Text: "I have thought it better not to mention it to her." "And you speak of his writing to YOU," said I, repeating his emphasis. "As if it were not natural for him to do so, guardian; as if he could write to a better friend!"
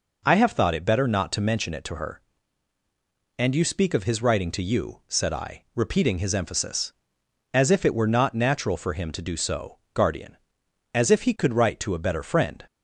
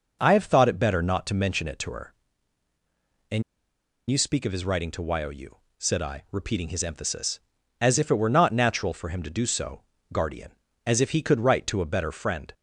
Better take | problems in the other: first | pauses between "And" and "you"; noticeable; at 3.4 s; 0.67 s long

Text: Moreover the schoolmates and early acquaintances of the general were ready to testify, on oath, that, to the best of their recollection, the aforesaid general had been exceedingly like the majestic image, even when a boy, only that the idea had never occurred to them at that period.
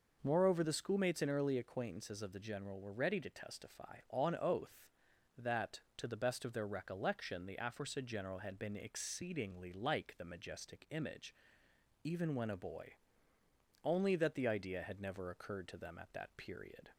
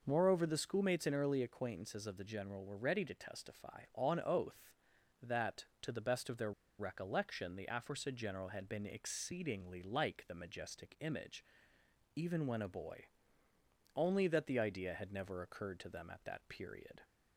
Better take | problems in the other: first | pauses between "their" and "recollection"; slight; at 6.5 s; 0.28 s long

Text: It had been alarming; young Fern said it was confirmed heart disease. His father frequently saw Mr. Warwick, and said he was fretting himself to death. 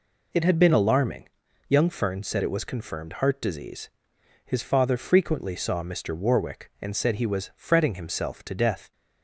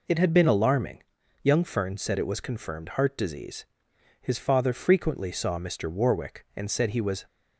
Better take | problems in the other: first | stops before "fretting himself to death"; at 7.2 s

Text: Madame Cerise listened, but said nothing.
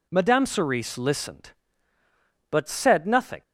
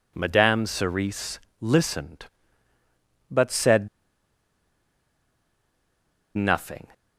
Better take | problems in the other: first | pauses between "Cerise" and "listened"; slight; at 1.4 s; 0.20 s long // pauses between "said" and "nothing"; strong; at 3.8 s; 2.4 s long

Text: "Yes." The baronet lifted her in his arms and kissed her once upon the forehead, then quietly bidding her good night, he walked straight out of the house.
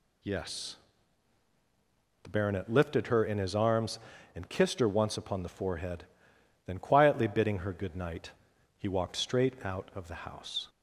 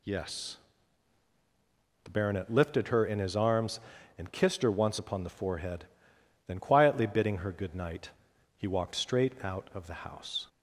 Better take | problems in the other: neither | none

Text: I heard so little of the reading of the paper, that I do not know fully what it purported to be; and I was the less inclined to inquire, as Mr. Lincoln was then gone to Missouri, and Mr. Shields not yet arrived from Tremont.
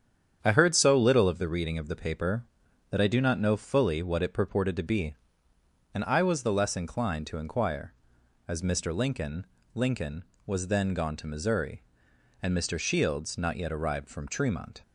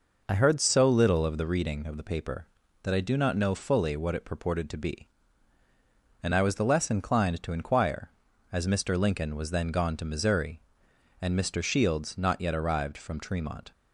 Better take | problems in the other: second | starts louder than the rest; strong; until 1.4 s; 8.5 dB // says "Lincoln" twice; at 9.7 s

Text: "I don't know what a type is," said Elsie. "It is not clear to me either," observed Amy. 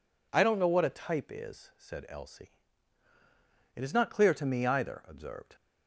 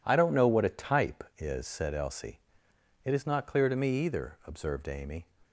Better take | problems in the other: second | stops before "Amy"; at 5.5 s

